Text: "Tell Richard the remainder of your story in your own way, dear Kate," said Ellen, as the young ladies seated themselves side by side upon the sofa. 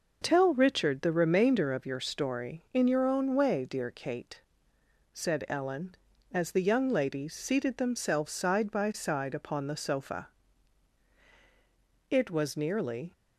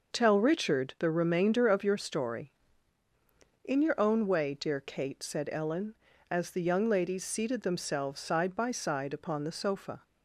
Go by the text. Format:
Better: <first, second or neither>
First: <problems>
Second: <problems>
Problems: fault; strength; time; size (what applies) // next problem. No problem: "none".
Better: second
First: goes on to say "It was nearly"; noticeable; from 12.0 s on; 1.0 s long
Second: none